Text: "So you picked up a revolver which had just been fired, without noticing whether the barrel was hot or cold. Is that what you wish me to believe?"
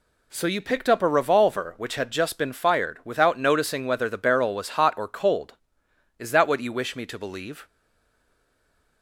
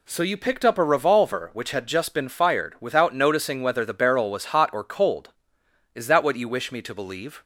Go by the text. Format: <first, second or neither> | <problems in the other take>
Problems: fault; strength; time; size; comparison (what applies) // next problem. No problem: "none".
second | stays silent after the last word; noticeable; from 7.6 s on; 1.4 s long